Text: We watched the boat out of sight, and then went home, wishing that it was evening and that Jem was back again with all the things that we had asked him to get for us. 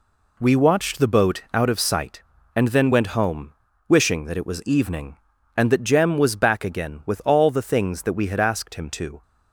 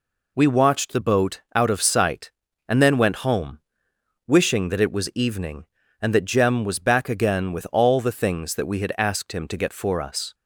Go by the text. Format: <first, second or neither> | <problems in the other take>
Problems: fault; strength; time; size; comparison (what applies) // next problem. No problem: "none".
second | stops before "get for us"; at 9.2 s